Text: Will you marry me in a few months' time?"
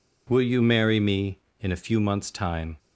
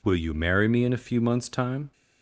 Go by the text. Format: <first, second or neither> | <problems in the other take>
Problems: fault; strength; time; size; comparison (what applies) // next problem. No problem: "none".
neither | none